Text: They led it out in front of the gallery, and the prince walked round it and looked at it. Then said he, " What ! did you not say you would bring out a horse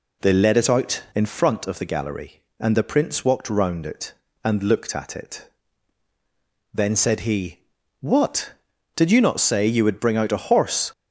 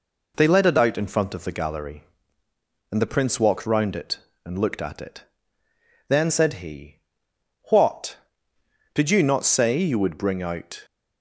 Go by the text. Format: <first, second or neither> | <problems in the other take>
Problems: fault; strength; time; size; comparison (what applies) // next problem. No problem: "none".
first | stops before "a horse"; at 10.8 s